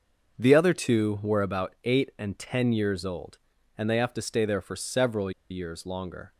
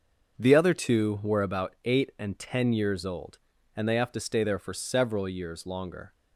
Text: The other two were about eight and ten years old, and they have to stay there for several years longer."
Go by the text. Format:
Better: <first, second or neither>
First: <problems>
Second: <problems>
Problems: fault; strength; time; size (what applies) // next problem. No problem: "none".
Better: second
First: starts louder than the rest; until 1.3 s; 6.5 dB // pauses between "several" and "years"; slight; at 5.3 s; 0.20 s long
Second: starts louder than the rest; until 1.3 s; 6 dB